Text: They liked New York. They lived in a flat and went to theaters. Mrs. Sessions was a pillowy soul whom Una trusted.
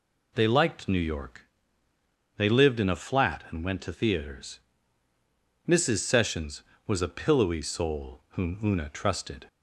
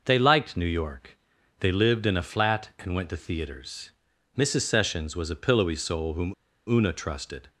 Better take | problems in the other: first | pauses between "whom" and "Una"; slight; at 6.3 s; 0.34 s long

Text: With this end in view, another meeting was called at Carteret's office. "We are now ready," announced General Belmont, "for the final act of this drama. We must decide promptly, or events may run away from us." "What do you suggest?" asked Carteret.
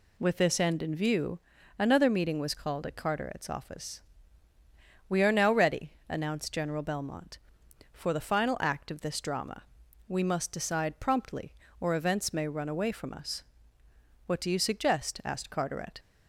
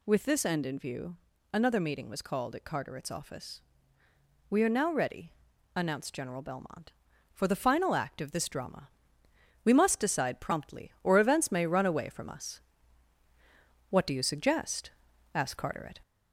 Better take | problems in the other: first | gets louder; slight; throughout; 2.5 dB

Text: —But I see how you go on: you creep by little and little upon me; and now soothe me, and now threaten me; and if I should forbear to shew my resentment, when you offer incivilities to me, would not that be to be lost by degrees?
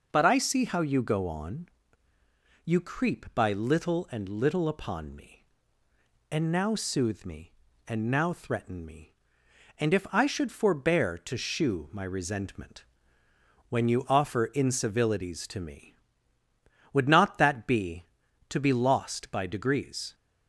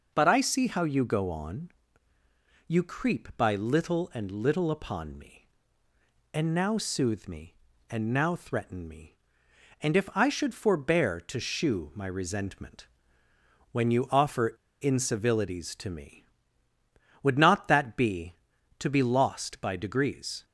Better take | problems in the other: first | pauses between "offer" and "incivilities"; slight; at 14.5 s; 0.27 s long

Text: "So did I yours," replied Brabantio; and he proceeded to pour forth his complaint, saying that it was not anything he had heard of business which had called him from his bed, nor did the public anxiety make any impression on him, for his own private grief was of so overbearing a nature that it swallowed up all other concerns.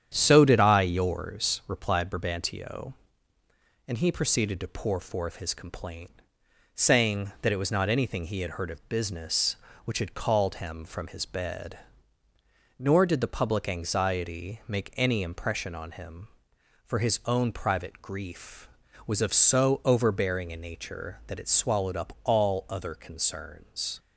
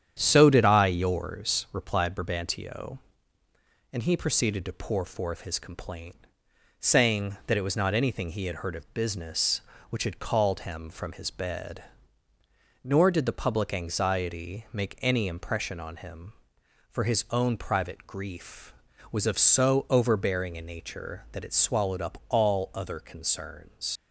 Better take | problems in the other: first | starts louder than the rest; strong; until 1.2 s; 9 dB; strong in the first // leaves "concerns" unfinished; at 23.9 s; 80 ms

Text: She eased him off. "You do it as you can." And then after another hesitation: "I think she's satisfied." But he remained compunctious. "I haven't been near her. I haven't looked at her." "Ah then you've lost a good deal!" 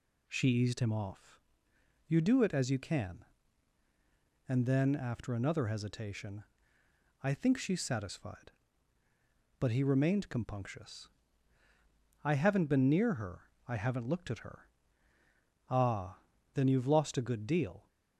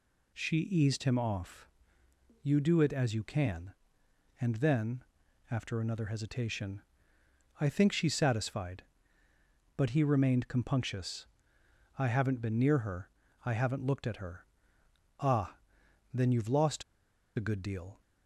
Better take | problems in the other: first | pauses between "then" and "after"; noticeable; at 5.0 s; 0.46 s long // pauses between "Ah" and "then"; noticeable; at 15.5 s; 0.56 s long; slight in the first // pauses between "lost" and "a"; noticeable; at 16.8 s; 0.53 s long

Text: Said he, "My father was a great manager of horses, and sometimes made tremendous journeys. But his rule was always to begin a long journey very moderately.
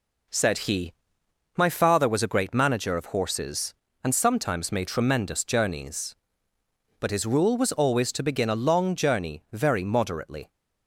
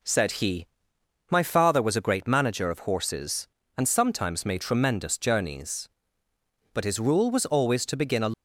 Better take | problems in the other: first | stops before "long journey very moderately"; at 8.3 s

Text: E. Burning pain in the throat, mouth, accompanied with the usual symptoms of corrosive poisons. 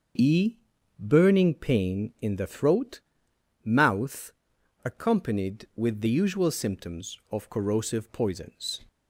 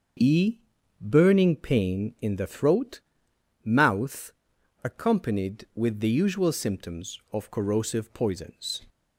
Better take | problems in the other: neither | starts louder than the rest; the same in both

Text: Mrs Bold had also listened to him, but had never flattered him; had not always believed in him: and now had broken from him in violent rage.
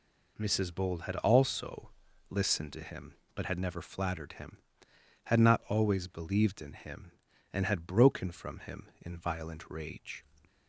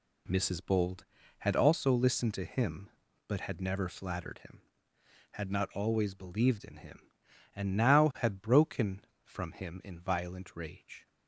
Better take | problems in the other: second | pauses between "also" and "listened"; at 1.9 s; 0.38 s long // skips "now"; at 7.6 s

